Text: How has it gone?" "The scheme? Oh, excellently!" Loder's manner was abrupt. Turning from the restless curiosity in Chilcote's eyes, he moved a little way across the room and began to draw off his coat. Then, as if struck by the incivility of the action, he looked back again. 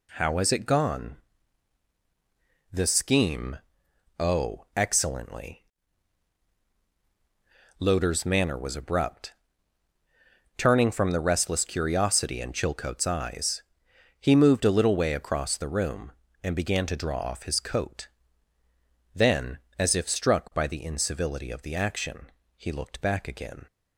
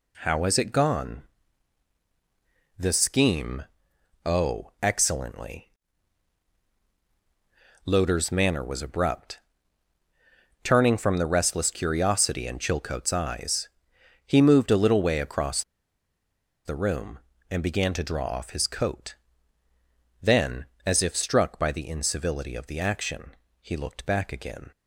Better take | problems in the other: first | pauses between "across" and "the"; at 15.6 s; 1.0 s long

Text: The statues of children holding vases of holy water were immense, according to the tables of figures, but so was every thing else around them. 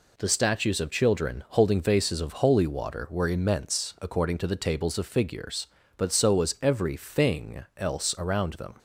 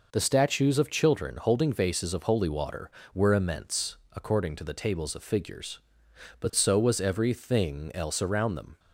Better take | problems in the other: neither | none

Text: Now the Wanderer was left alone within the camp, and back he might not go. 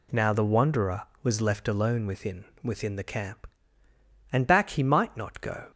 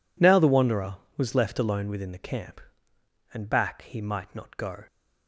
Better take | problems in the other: second | says "within" twice; at 2.6 s

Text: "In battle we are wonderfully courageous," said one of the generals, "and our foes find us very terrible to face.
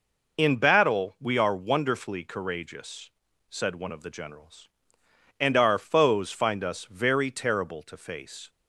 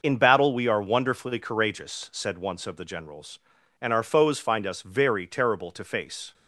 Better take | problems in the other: first | says "once" for "one"; at 2.3 s

